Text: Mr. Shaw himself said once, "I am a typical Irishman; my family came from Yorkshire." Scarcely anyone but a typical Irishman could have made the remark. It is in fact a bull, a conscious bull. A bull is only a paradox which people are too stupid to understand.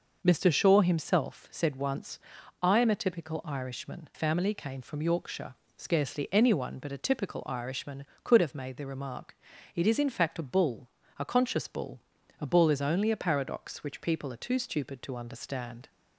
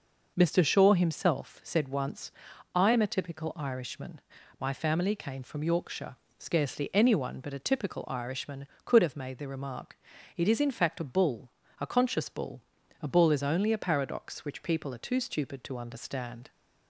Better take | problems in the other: second | skips "my"; at 4.1 s

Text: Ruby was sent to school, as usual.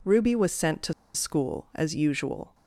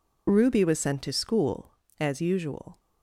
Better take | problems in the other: second | pauses between "to" and "school"; slight; at 0.9 s; 0.23 s long

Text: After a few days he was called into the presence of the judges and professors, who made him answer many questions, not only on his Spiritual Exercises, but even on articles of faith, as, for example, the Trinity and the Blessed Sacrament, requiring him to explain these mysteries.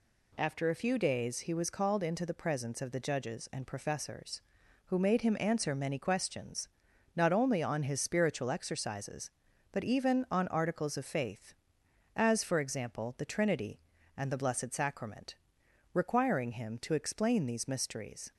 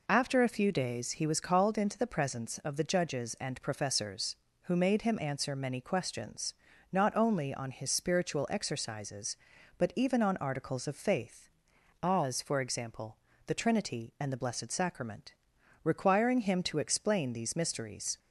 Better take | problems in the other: neither | none

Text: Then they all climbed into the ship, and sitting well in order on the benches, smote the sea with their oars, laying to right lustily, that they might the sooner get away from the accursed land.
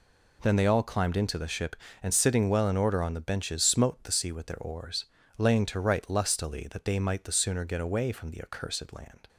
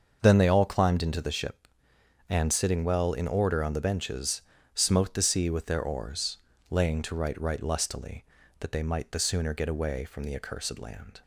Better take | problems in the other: first | starts louder than the rest; until 1.2 s; 6.5 dB // says "right" twice; at 7.3 s

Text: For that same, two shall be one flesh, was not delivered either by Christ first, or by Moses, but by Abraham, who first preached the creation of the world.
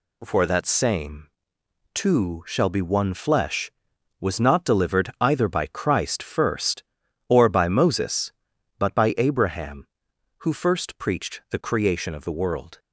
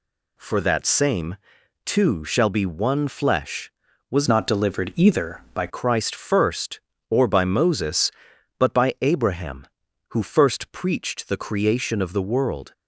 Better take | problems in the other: first | changes voice from "not" to "by"; from 4.2 to 5.6 s; 1.4 s long

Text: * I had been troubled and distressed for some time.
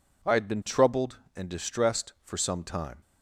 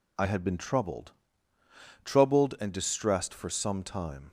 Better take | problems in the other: first | says "troubled" twice; at 2.0 s

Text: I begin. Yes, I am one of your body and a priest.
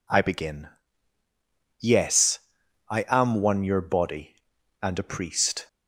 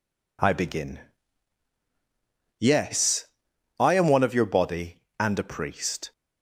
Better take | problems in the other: second | skips "of"; at 3.6 s

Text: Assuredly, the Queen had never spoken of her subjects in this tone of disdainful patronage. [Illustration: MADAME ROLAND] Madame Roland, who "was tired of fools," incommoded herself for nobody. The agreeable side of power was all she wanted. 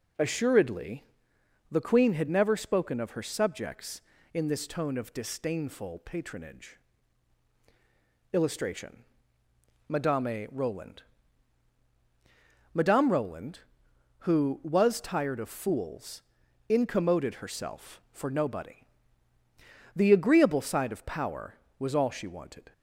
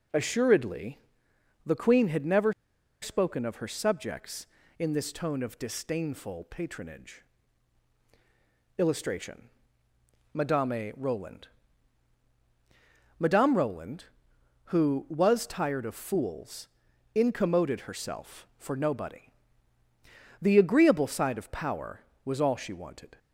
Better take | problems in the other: first | pauses between "never" and "spoken"; noticeable; at 2.5 s; 0.50 s long // pauses between "ROLAND" and "Madame"; strong; at 11.4 s; 1.7 s long; strong in the first

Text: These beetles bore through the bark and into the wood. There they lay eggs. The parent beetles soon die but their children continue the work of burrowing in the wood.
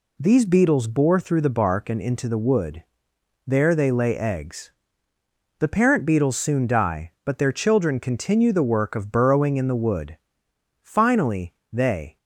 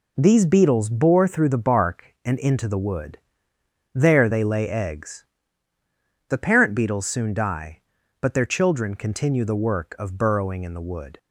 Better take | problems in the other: second | goes on to say "Finally they"; from 10.8 s on; 1.3 s long

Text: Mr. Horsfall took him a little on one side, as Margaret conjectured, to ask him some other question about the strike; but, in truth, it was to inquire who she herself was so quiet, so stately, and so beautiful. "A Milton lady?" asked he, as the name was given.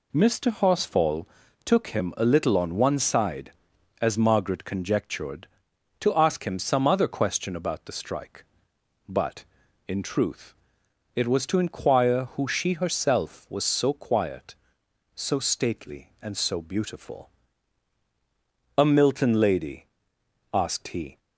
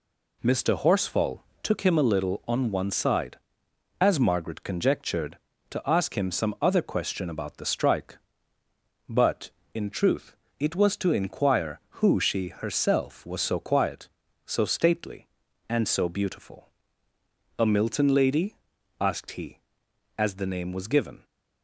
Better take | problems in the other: second | pauses between "Horsfall" and "took"; at 1.2 s; 0.38 s long; slight in the second // stops before "as the name was given"; at 21.1 s

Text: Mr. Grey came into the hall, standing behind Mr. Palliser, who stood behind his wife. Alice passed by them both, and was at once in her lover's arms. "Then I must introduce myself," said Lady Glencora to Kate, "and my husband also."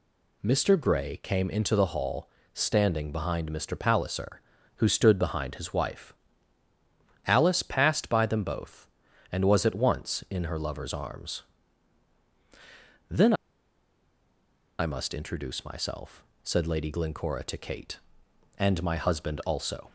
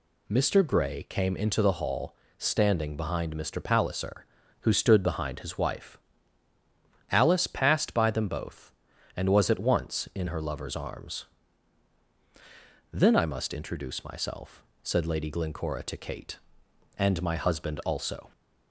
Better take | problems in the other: second | pauses between "Then" and "I"; strong; at 13.3 s; 1.4 s long

